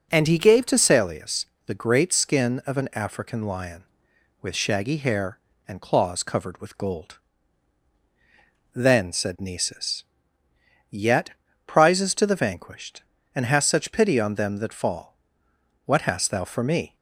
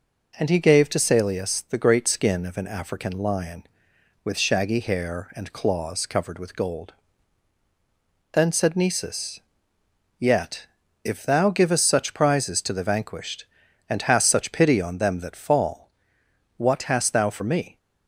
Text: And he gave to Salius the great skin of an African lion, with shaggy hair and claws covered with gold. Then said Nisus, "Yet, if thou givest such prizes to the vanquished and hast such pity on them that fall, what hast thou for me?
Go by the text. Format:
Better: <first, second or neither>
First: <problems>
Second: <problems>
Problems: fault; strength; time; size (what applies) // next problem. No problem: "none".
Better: second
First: pauses between "Salius" and "the"; slight; at 1.4 s; 0.20 s long // skips "if thou givest such"; at 11.4 s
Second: none